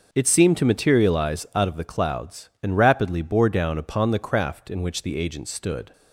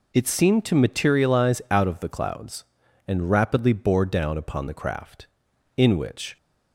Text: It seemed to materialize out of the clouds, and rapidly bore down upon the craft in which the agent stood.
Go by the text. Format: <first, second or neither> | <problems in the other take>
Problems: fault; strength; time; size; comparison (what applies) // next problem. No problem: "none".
first | stops before "the agent stood"; at 6.3 s